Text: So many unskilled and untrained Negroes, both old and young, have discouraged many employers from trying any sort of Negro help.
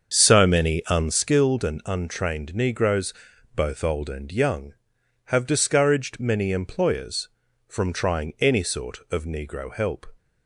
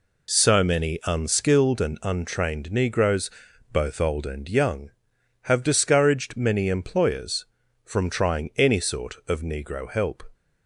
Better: second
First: starts louder than the rest; until 1.2 s; 7 dB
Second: none

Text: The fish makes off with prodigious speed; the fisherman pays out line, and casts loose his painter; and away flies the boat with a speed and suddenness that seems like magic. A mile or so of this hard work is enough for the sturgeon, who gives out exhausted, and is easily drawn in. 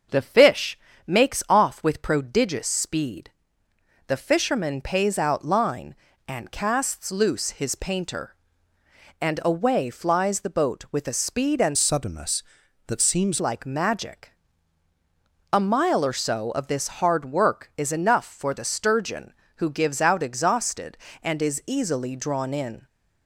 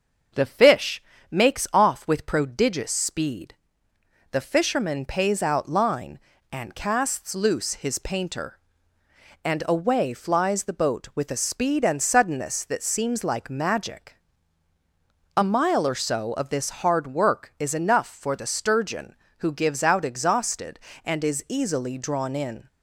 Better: second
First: starts louder than the rest; until 1.3 s; 6.5 dB // pauses between "fish" and "makes"; slight; at 0.7 s; 0.28 s long // changes voice from "suddenness" to "seems"; from 11.7 to 13.4 s; 1.7 s long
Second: starts louder than the rest; until 1.6 s; 6.5 dB // pauses between "fish" and "makes"; slight; at 1.0 s; 0.28 s long

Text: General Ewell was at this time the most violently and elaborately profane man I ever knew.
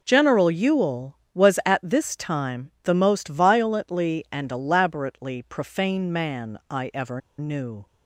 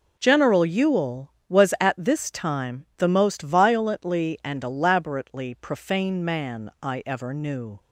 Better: second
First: pauses between "ever" and "knew"; slight; at 7.2 s; 0.17 s long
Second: none

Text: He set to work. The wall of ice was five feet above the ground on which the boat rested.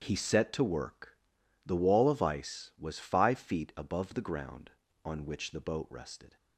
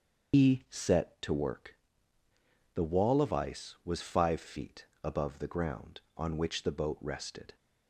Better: first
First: starts louder than the rest; strong; until 1.0 s; 8 dB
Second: loses the start of "He"; at 0.3 s; 125 ms // starts louder than the rest; until 1.4 s; 6.5 dB // pauses between "feet" and "above"; slight; at 4.8 s; 0.16 s long

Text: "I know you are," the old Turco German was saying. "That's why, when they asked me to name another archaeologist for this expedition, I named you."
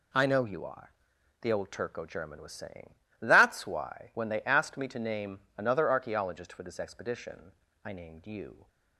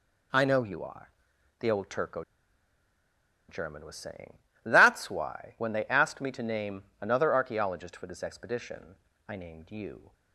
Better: first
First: none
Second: pauses between "Turco" and "German"; strong; at 2.2 s; 1.2 s long

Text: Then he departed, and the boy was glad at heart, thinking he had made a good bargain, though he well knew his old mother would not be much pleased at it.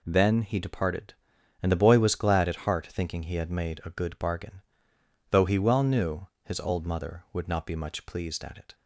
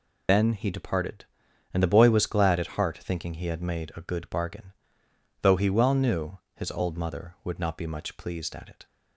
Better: first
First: pauses between "knew" and "his"; slight; at 6.2 s; 0.16 s long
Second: loses the start of "Then"; at 0.2 s; 135 ms // pauses between "knew" and "his"; slight; at 6.3 s; 0.16 s long

